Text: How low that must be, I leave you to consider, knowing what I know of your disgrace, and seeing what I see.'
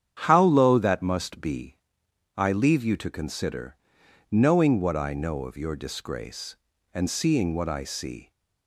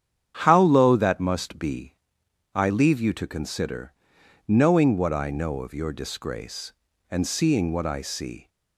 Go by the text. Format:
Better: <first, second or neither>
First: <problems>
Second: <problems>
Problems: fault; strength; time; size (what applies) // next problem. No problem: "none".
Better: neither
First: starts louder than the rest; strong; until 1.2 s; 8.5 dB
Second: starts louder than the rest; strong; until 1.4 s; 9 dB